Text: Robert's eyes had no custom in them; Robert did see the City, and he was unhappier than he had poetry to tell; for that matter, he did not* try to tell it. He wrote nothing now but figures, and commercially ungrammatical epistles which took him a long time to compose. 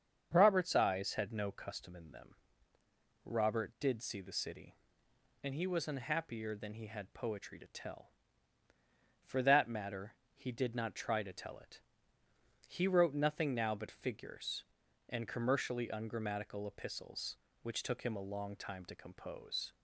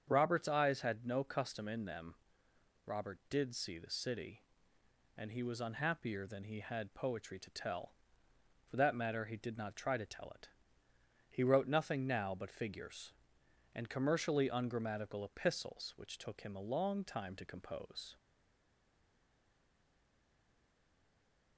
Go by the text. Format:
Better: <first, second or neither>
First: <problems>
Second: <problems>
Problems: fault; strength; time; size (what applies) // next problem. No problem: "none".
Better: first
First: starts louder than the rest; strong; until 1.3 s; 7.5 dB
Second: starts louder than the rest; strong; until 1.0 s; 7.5 dB // stays silent after the last word; strong; from 18.1 s on; 3.4 s long